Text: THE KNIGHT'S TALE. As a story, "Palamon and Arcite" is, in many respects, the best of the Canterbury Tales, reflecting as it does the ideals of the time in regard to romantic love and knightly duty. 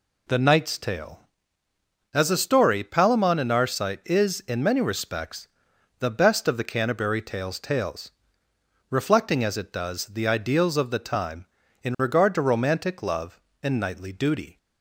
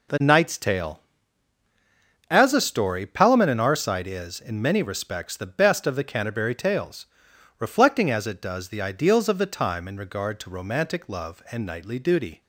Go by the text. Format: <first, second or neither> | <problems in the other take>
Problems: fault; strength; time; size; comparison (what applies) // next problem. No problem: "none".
second | says "Tales" twice; at 7.6 s